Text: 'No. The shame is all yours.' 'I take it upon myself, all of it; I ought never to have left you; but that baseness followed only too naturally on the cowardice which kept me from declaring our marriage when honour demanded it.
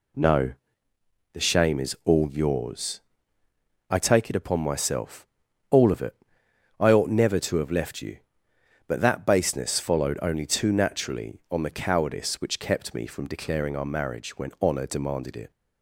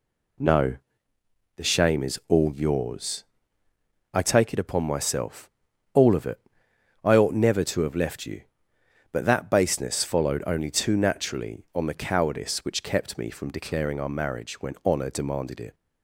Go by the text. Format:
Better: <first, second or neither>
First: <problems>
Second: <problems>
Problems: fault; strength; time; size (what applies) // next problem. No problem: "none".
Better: neither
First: none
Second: none